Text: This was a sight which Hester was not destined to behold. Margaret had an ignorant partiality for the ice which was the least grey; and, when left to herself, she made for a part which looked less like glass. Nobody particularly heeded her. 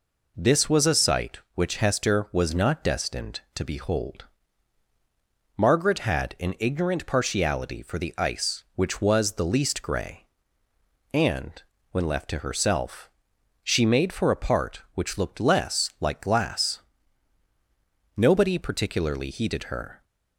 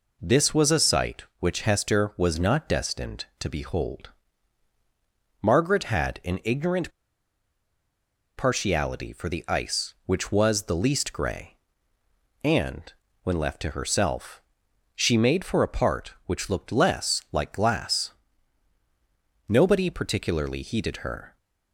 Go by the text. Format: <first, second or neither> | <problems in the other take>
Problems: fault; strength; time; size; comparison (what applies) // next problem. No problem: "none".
first | pauses between "ignorant" and "partiality"; strong; at 6.8 s; 1.4 s long